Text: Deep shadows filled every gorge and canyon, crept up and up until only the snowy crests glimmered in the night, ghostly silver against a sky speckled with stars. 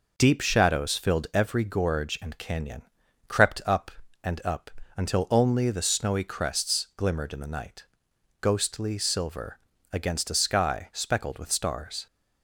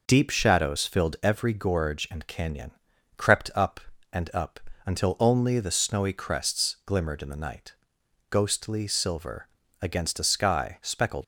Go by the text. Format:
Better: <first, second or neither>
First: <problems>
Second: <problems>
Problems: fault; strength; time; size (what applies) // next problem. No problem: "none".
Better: first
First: pauses between "up" and "until"; slight; at 4.7 s; 0.26 s long // pauses between "silver" and "against"; slight; at 9.5 s; 0.34 s long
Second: pauses between "up" and "until"; slight; at 4.5 s; 0.26 s long // pauses between "silver" and "against"; slight; at 9.4 s; 0.34 s long // stops before "with stars"; at 11.2 s